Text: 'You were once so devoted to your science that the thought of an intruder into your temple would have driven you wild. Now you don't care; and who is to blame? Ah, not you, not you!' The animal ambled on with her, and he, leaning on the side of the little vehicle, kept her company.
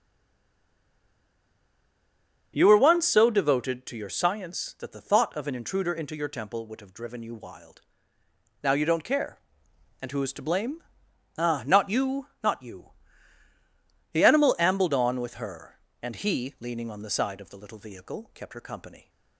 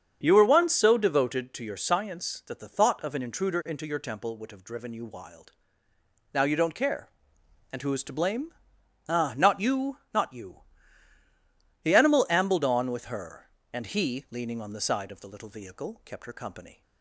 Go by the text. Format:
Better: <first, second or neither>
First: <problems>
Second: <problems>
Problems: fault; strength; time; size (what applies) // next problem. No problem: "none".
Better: second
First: stays silent before the first word; until 2.5 s; 2.5 s long // starts louder than the rest; strong; until 3.5 s; 7.5 dB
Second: starts louder than the rest; strong; until 1.2 s; 7.5 dB